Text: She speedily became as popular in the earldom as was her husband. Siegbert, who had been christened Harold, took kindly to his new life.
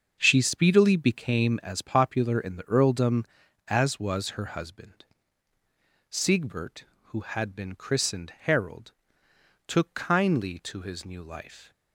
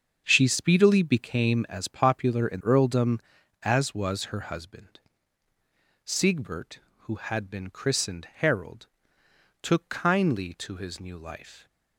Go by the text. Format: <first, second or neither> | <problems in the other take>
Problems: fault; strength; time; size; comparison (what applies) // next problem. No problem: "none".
first | starts louder than the rest; until 1.2 s; 7 dB; also in the first // skips "the"; at 2.6 s